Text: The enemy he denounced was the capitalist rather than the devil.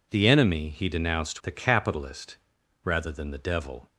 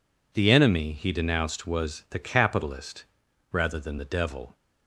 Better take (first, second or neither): second